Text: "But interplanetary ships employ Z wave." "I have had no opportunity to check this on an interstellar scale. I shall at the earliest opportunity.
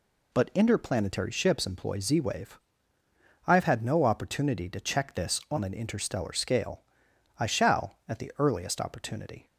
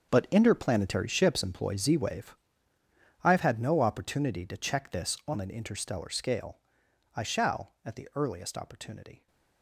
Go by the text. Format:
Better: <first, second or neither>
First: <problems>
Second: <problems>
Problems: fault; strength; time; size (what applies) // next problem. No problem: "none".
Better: first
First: none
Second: gets quieter; strong; throughout; 15 dB